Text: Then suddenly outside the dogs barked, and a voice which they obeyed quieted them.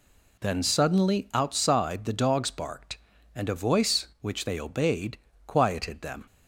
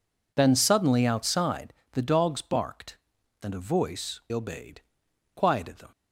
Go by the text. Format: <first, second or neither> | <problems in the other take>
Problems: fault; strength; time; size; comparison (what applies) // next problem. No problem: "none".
first | pauses between "outside" and "the"; slight; at 1.7 s; 0.20 s long // skips "which they"; at 4.2 s // pauses between "obeyed" and "quieted"; noticeable; at 4.8 s; 0.52 s long; slight in the first